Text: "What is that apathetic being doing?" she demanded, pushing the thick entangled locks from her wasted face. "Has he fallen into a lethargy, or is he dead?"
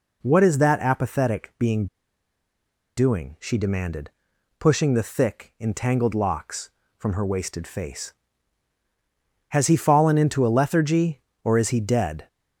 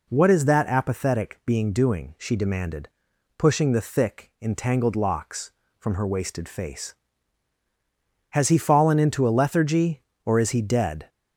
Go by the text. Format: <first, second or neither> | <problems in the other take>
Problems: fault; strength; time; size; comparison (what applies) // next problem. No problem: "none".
second | pauses between "being" and "doing"; at 1.8 s; 1.1 s long